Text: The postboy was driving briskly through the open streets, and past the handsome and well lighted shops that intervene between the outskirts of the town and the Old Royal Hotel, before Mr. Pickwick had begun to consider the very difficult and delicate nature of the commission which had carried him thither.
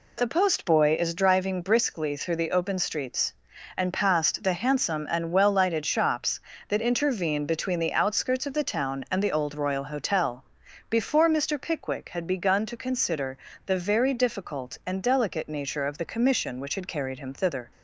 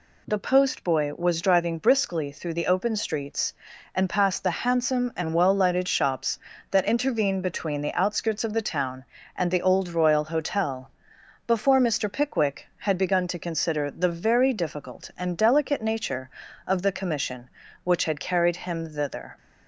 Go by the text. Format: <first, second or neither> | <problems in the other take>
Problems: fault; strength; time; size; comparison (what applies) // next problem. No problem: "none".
second | says "is" for "was"; at 0.9 s // pauses between "consider" and "the"; slight; at 13.3 s; 0.28 s long